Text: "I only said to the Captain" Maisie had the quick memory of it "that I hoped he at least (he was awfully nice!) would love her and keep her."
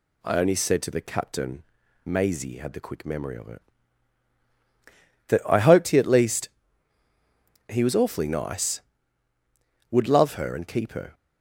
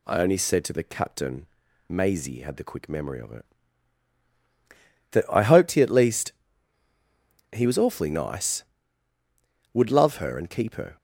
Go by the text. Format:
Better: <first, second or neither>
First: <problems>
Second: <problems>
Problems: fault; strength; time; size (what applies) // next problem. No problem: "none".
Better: neither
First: pauses between "Captain" and "Maisie"; at 1.6 s; 0.42 s long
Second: pauses between "Captain" and "Maisie"; at 1.4 s; 0.42 s long